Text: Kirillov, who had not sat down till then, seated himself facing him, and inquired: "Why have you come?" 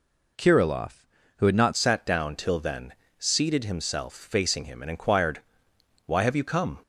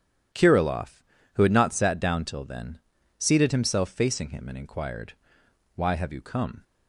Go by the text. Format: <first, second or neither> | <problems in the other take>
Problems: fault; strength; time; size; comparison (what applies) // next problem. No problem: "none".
second | changes voice at "sat"; from 1.7 s on; 5.0 s long